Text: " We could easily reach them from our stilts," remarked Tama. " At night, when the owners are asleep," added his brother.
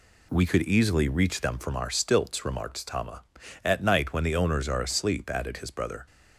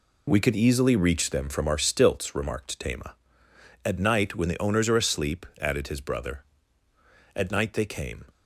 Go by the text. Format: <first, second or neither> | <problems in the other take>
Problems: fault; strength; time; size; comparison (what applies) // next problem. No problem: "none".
first | goes on to say "At night they came"; noticeable; from 7.3 s on; 0.92 s long